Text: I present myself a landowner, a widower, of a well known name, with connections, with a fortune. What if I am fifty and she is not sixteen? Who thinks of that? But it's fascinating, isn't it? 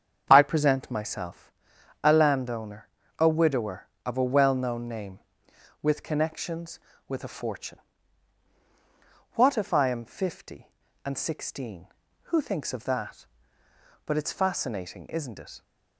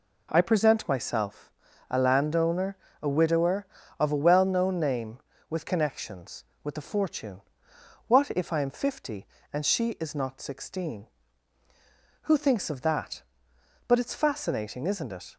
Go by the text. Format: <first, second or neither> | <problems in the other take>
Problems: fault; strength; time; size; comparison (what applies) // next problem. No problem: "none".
second | starts louder than the rest; strong; until 1.3 s; 7.5 dB // pauses between "myself" and "a"; noticeable; at 1.5 s; 0.52 s long; also in the second // skips "she is not"; at 11.1 s